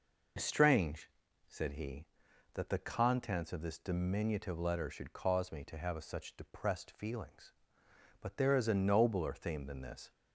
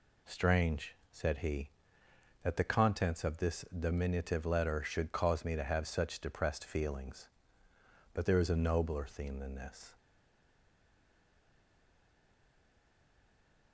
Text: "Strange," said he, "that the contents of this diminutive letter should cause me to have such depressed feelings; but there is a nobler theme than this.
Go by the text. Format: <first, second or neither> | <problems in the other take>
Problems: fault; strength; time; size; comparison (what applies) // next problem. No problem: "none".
first | stays silent after the last word; strong; from 9.9 s on; 3.8 s long